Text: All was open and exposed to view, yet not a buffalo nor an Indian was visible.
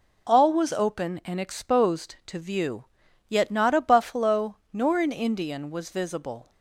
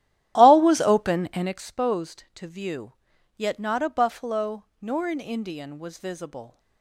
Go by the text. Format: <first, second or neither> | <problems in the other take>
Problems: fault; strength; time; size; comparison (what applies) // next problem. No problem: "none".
first | starts louder than the rest; strong; until 1.6 s; 12.5 dB // pauses between "buffalo" and "nor"; slight; at 4.6 s; 0.18 s long; slight in the first